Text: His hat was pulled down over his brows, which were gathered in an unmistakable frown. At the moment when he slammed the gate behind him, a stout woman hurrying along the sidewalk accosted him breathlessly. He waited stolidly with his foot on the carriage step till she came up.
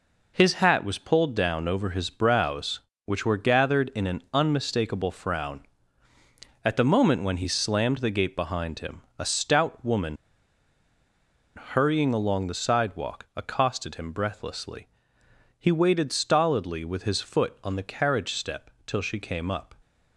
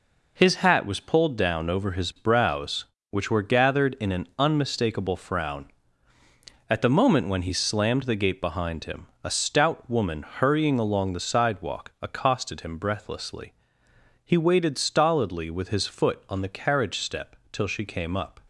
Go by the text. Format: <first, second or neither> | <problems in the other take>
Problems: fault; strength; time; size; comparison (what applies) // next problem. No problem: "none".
second | pauses between "woman" and "hurrying"; strong; at 10.1 s; 1.3 s long // pauses between "step" and "till"; slight; at 18.7 s; 0.16 s long; slight in the second